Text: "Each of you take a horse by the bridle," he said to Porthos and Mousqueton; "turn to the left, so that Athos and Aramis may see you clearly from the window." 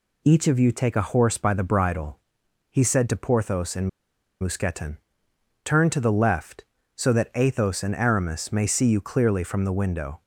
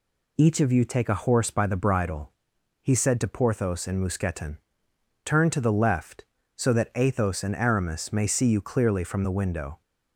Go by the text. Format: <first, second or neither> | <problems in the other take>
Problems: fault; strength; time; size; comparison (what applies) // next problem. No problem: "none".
second | pauses between "and" and "Mousqueton"; noticeable; at 3.8 s; 0.51 s long